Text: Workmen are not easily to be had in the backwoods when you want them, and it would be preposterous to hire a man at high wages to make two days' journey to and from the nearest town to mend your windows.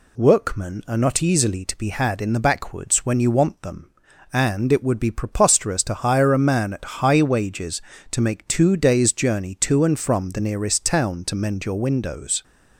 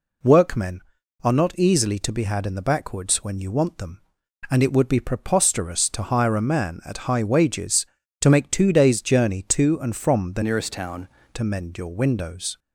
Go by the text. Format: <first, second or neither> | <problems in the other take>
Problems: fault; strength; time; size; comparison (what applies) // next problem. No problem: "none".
first | changes voice from "nearest" to "town"; from 10.4 to 11.0 s; 0.6 s long